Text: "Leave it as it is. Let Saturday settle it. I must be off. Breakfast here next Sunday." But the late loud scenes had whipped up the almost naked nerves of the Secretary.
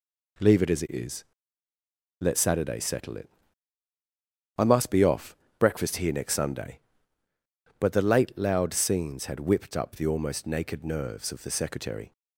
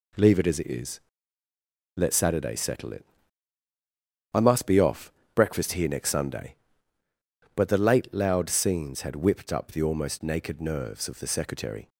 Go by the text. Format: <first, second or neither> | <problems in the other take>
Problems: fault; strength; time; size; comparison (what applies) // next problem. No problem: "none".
neither | none